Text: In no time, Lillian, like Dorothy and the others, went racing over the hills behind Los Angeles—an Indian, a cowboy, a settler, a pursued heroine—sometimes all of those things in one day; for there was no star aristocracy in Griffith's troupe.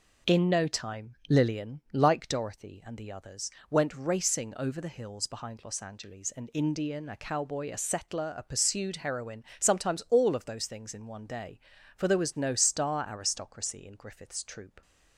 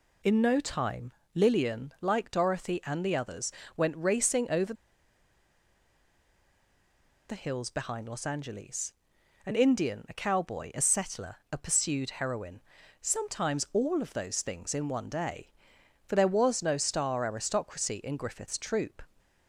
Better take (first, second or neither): first